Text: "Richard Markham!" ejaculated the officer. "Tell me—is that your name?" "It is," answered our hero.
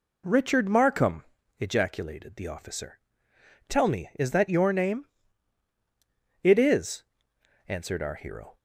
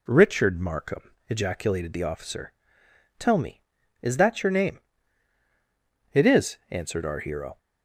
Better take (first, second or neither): neither